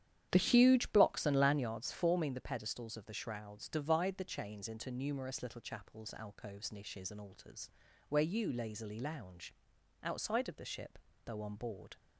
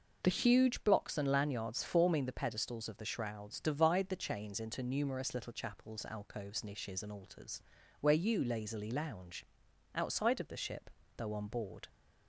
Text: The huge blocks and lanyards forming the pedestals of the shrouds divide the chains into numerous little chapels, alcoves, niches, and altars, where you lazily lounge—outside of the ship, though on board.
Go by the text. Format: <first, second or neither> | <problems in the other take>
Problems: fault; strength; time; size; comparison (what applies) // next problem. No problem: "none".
second | starts louder than the rest; strong; until 1.8 s; 10 dB